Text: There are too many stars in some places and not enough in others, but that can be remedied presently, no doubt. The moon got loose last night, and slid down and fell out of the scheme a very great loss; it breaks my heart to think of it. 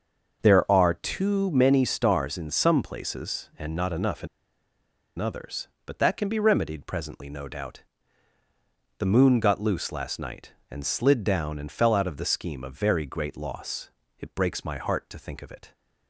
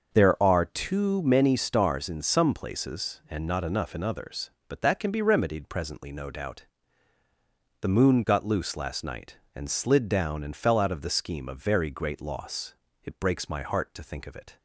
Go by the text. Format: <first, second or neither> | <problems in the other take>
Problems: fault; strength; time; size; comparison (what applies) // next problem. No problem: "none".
second | starts louder than the rest; until 1.4 s; 6.5 dB; also in the second // pauses between "in" and "others"; noticeable; at 4.2 s; 0.91 s long